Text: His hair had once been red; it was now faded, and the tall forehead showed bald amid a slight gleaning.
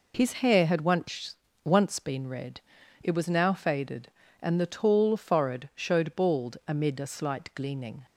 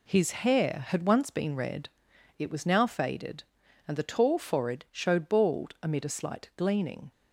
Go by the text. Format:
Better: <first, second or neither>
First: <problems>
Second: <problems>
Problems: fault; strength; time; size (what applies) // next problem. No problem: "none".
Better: second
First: says "once" twice; at 1.6 s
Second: none